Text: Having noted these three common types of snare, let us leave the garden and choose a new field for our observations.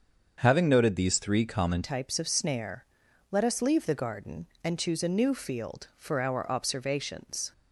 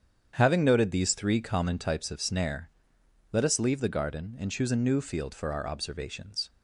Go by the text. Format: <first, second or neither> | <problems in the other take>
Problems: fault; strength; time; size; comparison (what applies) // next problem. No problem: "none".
second | starts louder than the rest; until 1.3 s; 7 dB; strong in the second // changes voice at "types"; from 1.8 s on; 5.7 s long